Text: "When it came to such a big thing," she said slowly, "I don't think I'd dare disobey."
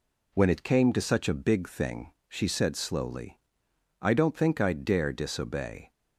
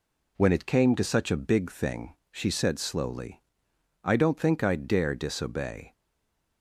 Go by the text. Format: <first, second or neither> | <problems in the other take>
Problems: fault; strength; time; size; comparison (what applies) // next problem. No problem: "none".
first | stays silent after the last word; slight; from 5.9 s on; 0.7 s long